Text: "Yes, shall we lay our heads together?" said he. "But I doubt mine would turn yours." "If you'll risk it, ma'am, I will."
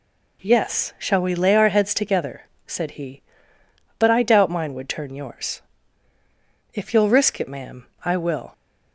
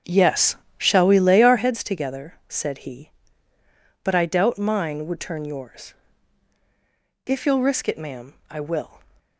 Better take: first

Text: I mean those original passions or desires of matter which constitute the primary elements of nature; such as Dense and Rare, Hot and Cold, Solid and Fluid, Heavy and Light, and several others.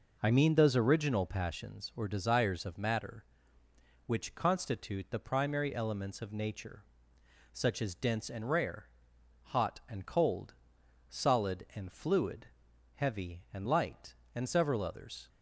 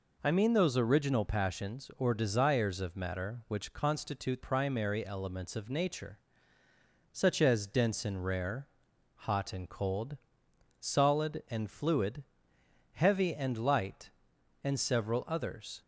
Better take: first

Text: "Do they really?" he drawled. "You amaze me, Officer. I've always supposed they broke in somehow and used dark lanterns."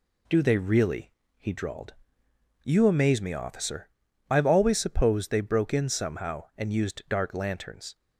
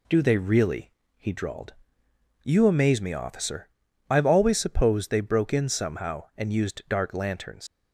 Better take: first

